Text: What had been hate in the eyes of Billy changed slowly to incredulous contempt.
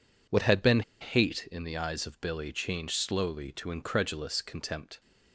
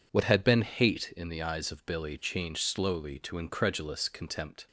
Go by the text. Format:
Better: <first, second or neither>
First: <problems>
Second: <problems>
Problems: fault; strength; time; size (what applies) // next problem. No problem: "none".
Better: second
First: pauses between "been" and "hate"; slight; at 0.8 s; 0.19 s long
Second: none